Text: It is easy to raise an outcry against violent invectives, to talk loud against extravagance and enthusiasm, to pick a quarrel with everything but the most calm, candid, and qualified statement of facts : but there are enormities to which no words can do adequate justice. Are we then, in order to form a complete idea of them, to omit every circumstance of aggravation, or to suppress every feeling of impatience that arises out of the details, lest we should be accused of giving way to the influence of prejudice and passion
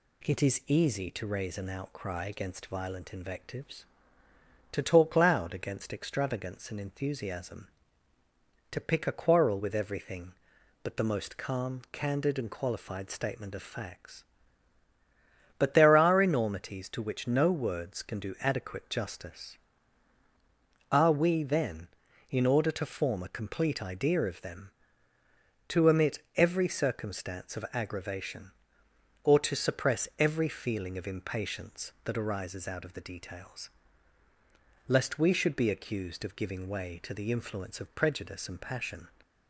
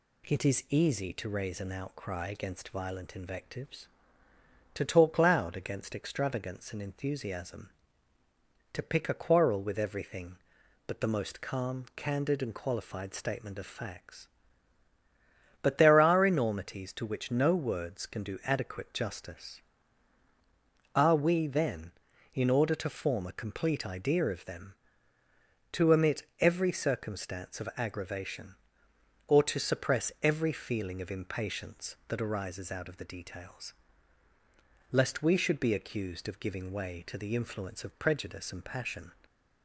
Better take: neither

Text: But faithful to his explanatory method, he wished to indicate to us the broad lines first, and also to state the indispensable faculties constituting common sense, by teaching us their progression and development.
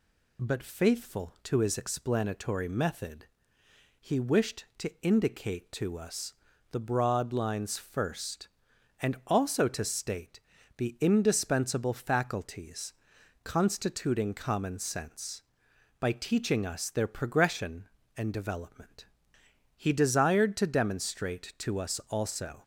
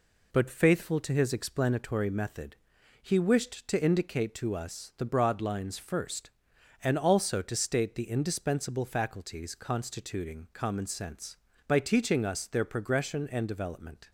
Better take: second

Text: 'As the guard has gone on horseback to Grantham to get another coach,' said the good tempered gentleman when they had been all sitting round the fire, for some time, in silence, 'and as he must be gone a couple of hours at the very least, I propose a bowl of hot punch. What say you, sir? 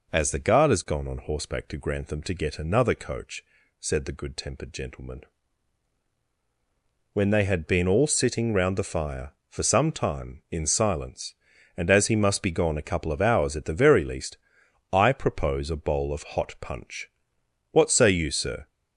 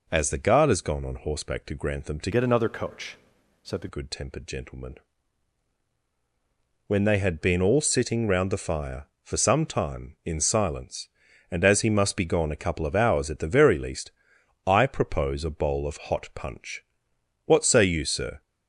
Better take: first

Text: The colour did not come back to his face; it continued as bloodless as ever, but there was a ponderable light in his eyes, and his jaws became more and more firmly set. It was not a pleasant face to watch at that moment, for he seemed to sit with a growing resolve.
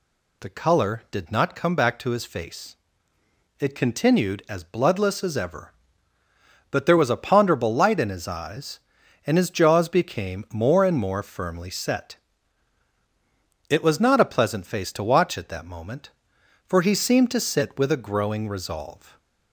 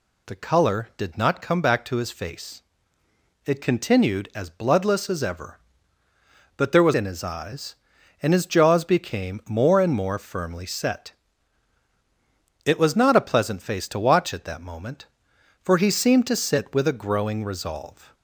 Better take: first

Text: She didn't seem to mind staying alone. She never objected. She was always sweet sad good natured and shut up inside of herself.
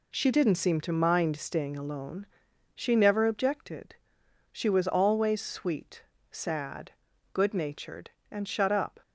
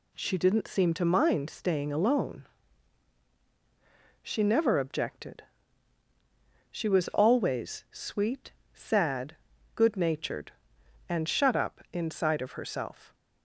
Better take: second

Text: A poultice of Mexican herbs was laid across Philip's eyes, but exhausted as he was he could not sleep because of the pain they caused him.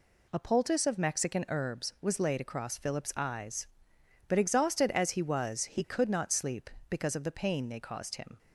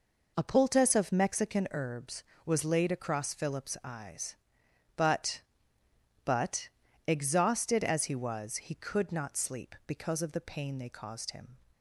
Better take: first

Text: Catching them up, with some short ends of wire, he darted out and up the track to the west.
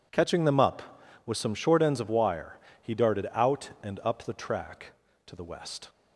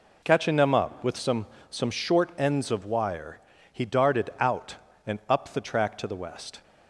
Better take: first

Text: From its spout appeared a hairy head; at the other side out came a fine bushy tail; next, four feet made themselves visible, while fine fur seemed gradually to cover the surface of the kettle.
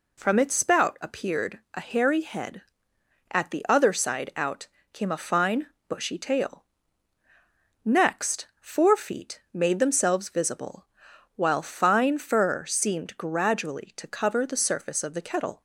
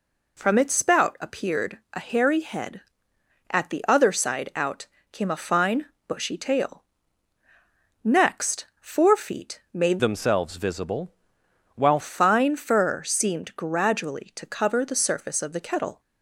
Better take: first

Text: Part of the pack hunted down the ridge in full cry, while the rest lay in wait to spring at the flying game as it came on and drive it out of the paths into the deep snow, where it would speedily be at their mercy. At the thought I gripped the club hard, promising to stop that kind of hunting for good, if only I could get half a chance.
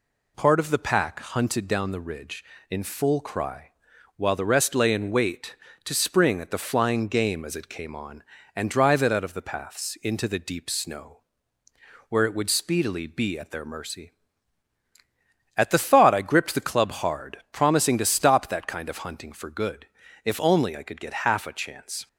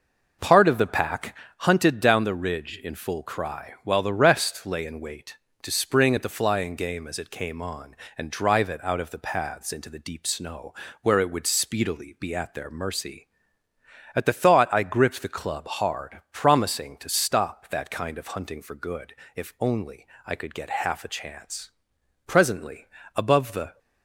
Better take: first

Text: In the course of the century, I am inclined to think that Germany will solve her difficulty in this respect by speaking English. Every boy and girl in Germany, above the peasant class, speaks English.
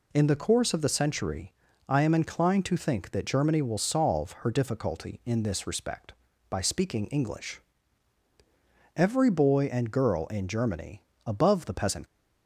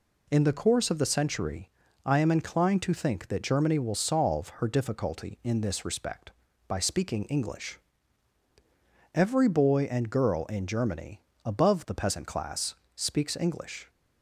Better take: second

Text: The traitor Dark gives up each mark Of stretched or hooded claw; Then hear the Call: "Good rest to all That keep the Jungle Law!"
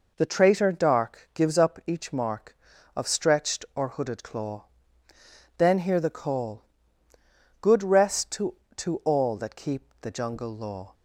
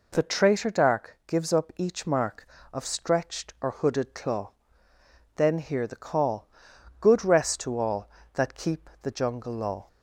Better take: second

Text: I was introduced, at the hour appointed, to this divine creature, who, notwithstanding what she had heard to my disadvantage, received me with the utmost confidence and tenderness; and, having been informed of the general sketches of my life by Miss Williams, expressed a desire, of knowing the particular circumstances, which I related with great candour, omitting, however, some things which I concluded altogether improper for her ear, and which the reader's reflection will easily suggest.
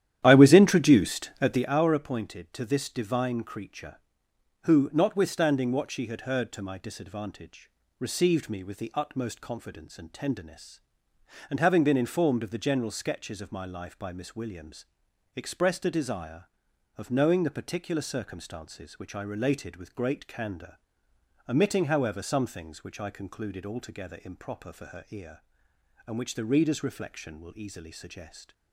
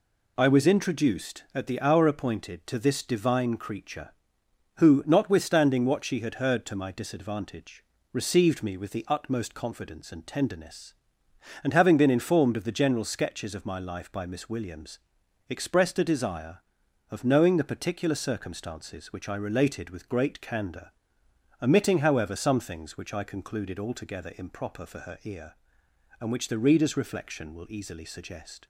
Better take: second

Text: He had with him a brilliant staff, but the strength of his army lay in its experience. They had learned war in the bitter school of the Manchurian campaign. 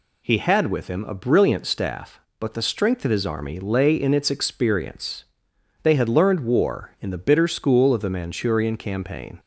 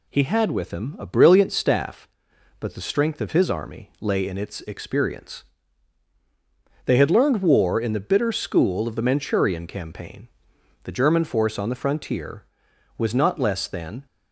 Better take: first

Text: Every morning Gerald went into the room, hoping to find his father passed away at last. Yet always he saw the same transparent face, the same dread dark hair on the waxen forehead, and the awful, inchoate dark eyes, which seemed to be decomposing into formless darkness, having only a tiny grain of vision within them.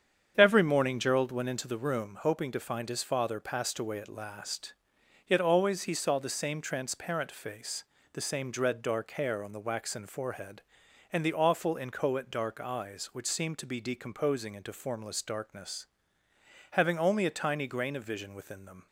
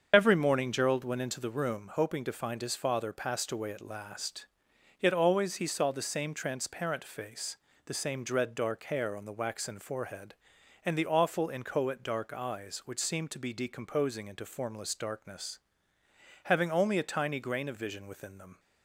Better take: first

